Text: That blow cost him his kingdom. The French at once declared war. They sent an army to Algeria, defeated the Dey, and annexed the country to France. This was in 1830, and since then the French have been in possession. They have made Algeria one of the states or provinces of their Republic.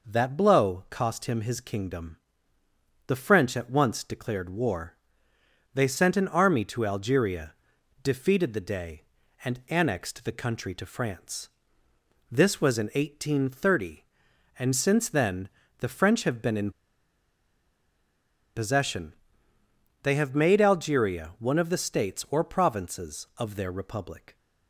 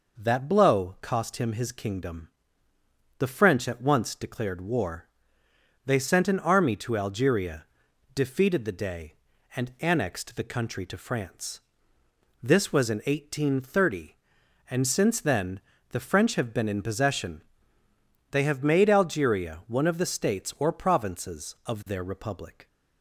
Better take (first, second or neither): second